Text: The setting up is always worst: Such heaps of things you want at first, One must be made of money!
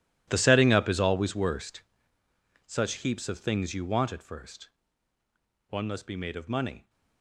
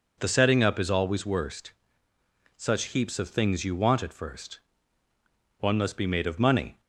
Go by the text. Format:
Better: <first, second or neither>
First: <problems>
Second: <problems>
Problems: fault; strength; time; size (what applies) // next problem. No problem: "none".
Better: second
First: gets quieter; strong; throughout; 18 dB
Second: none